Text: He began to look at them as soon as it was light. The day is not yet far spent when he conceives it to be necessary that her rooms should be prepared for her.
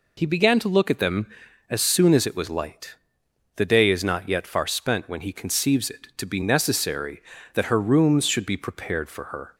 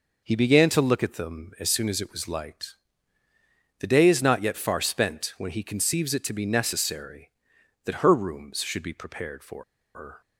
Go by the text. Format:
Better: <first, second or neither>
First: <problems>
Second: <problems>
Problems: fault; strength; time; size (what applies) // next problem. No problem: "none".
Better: first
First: none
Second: pauses between "for" and "her"; slight; at 9.6 s; 0.31 s long